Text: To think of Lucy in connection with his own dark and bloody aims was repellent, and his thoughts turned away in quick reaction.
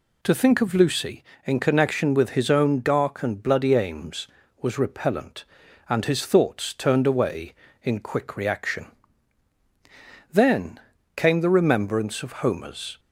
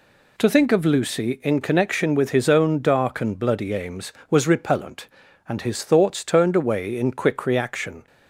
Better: second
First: goes on to say "Then came the remembrance of Homer's"; strong; from 10.3 s on; 2.6 s long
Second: none

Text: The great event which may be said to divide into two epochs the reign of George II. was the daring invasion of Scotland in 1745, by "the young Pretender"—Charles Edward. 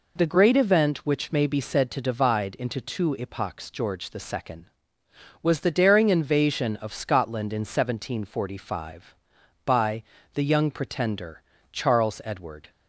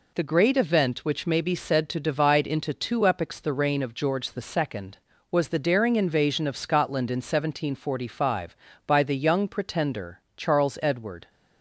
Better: second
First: skips "the reign of"; at 3.6 s // pauses between "by" and "the"; slight; at 10.0 s; 0.30 s long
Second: none

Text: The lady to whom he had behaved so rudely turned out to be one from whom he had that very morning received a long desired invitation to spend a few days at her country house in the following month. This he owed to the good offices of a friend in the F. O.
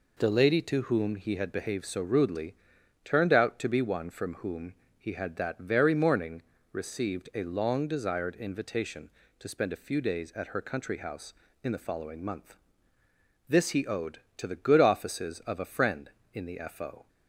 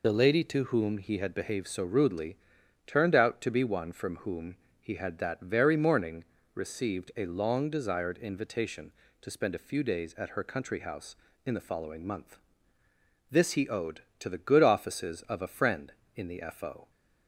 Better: first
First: pauses between "rudely" and "turned"; noticeable; at 2.5 s; 0.48 s long // pauses between "whom" and "he"; slight; at 4.7 s; 0.24 s long // pauses between "morning" and "received"; slight; at 6.4 s; 0.30 s long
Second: loses the start of "The"; at 0.0 s; 40 ms // pauses between "rudely" and "turned"; noticeable; at 2.3 s; 0.48 s long // pauses between "whom" and "he"; slight; at 4.5 s; 0.24 s long // pauses between "morning" and "received"; slight; at 6.2 s; 0.30 s long

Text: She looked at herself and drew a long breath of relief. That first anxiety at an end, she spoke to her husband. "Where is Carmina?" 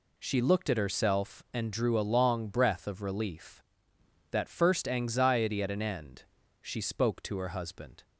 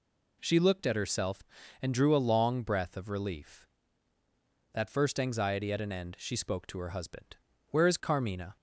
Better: second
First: stops before "Where is Carmina"; at 8.0 s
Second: none

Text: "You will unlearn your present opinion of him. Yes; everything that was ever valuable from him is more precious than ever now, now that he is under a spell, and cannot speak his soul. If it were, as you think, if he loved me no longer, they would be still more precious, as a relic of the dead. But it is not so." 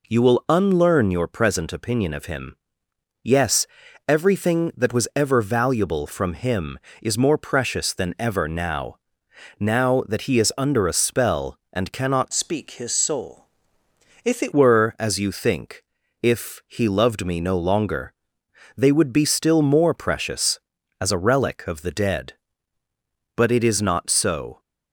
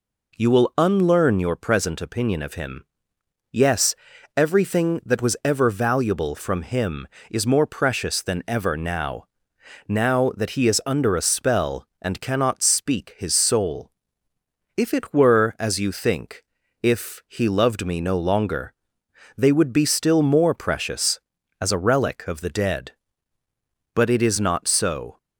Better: second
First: changes voice from "speak" to "it"; from 12.3 to 14.5 s; 2.2 s long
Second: none

